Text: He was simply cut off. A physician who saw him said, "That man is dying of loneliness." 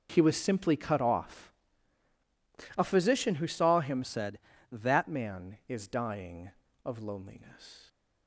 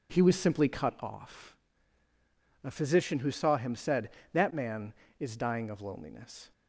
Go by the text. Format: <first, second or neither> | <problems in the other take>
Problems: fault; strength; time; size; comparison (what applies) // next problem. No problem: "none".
second | changes voice from "said" to "That"; from 4.0 to 5.0 s; 1.0 s long